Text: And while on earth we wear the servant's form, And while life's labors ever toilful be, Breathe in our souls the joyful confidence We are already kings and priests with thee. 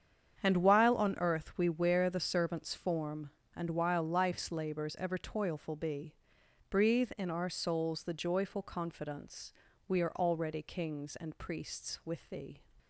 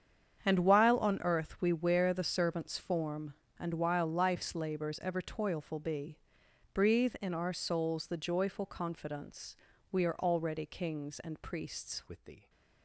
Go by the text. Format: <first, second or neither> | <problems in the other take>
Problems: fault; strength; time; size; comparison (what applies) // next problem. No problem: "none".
first | starts louder than the rest; strong; until 1.4 s; 8 dB; strong in the first // pauses between "confidence" and "We"; slight; at 9.5 s; 0.36 s long; slight in the first // changes voice at "with"; from 12.0 s on; 0.4 s long